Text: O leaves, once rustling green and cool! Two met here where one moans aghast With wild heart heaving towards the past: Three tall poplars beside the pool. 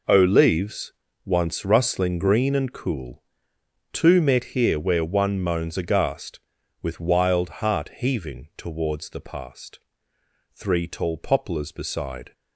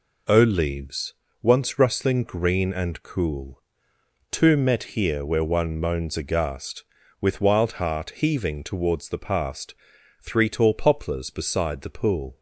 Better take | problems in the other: second | stops before "the pool"; at 12.3 s

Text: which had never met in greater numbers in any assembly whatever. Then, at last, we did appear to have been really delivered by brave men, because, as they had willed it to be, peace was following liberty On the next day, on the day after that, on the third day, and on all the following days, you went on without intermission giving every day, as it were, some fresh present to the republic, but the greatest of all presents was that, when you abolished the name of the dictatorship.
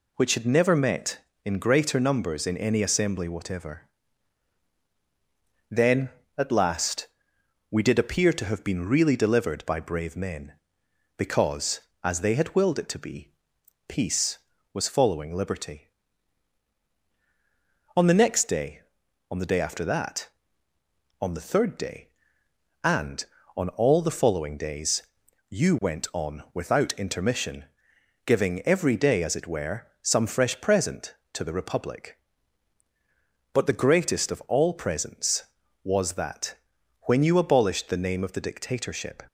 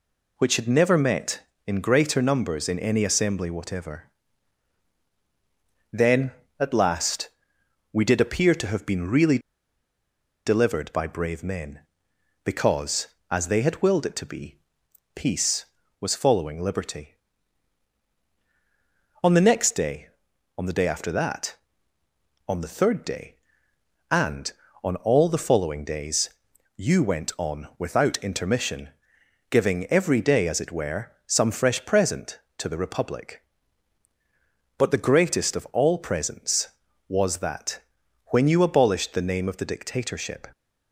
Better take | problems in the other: first | pauses between "really" and "delivered"; at 9.3 s; 1.0 s long // pauses between "intermission" and "giving"; noticeable; at 28.8 s; 0.62 s long; noticeable in the first

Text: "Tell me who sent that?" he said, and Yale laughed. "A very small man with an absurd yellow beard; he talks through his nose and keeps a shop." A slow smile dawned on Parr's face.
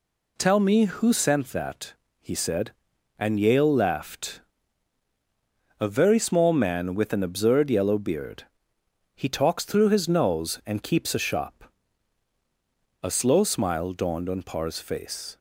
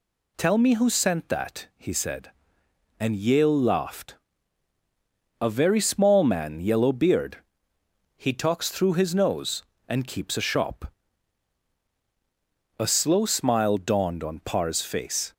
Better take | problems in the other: first | skips "with an absurd"; at 6.6 s

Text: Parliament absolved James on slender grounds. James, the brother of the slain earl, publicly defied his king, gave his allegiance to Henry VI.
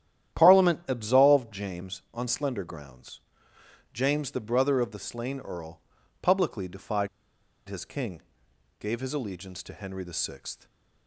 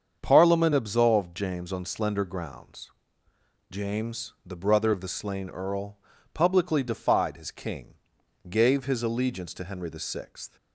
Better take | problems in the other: second | starts louder than the rest; strong; until 1.4 s; 11 dB; strong in the second // pauses between "defied" and "his"; noticeable; at 7.0 s; 0.61 s long

